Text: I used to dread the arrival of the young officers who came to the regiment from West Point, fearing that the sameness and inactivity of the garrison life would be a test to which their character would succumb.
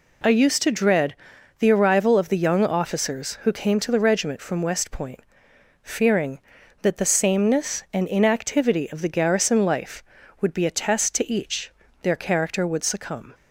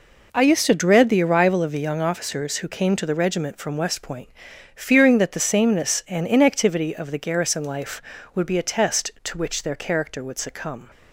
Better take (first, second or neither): second